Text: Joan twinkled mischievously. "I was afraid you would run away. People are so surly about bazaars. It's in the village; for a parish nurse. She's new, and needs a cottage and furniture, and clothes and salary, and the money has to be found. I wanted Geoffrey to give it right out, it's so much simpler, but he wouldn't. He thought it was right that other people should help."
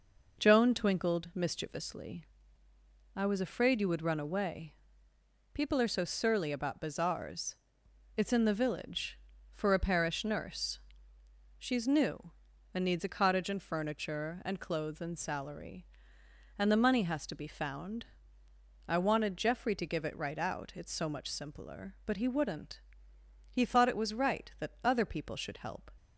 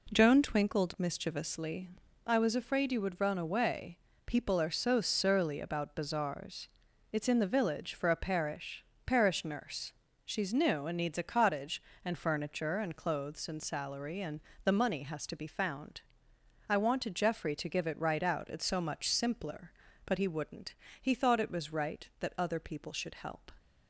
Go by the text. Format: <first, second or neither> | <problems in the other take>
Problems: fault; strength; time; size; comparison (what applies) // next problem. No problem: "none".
first | says "parish" twice; at 9.0 s // pauses between "and" and "the"; slight; at 14.3 s; 0.24 s long